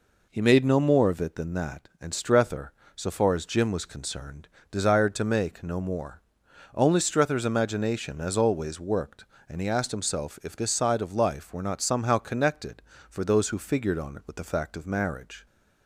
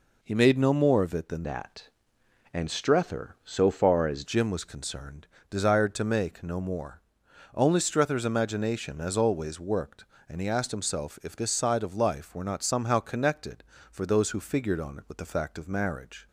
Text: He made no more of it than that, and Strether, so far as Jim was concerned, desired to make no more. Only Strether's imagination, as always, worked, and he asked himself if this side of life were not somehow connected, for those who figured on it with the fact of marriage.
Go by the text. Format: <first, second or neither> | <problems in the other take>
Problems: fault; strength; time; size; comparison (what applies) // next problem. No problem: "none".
first | changes voice from "that" to "as"; from 1.4 to 4.2 s; 2.8 s long